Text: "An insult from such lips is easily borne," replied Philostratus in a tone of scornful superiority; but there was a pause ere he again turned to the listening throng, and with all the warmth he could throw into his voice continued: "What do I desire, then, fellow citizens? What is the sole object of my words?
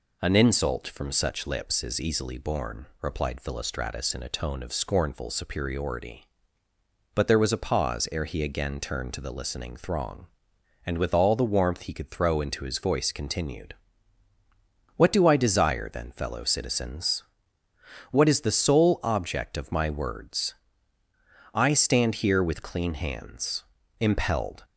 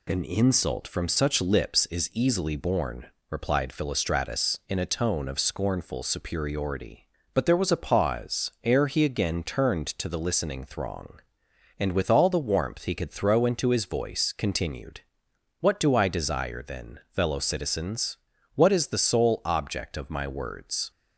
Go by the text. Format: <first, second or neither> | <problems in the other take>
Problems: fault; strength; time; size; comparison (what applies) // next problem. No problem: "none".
second | goes on to say "I stand here with clean hands impelled"; strong; from 21.5 s on; 3.1 s long